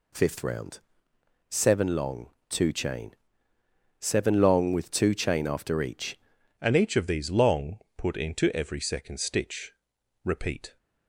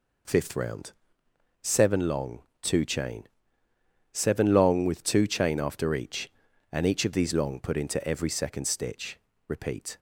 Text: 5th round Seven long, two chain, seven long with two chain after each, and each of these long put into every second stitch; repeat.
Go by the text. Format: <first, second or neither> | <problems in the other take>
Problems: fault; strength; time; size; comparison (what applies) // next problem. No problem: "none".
second | pauses between "round" and "Seven"; noticeable; at 0.7 s; 0.72 s long; noticeable in the second // changes voice at "and"; from 6.6 s on; 4.1 s long // pauses between "long" and "put"; slight; at 7.7 s; 0.22 s long